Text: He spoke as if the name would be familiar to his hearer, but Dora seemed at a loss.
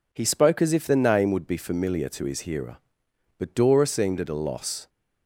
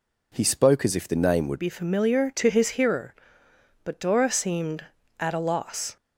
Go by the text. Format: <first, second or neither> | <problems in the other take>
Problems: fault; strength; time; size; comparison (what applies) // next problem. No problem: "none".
first | changes voice at "be"; from 1.5 s on; 4.4 s long